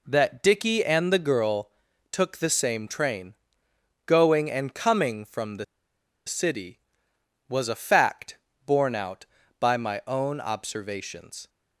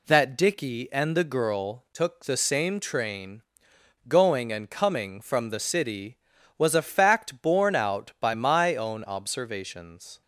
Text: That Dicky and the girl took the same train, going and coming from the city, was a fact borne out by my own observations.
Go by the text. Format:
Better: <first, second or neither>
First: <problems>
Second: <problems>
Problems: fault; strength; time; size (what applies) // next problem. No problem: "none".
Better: second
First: pauses between "girl" and "took"; at 1.6 s; 0.42 s long // pauses between "the" and "city"; noticeable; at 5.6 s; 0.62 s long // pauses between "fact" and "borne"; slight; at 8.3 s; 0.28 s long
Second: none